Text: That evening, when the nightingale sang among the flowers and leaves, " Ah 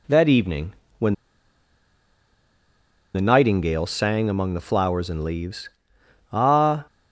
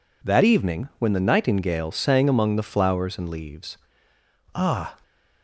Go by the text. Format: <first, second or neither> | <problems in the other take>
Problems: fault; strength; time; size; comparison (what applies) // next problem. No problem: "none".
second | pauses between "when" and "the"; strong; at 1.1 s; 2.0 s long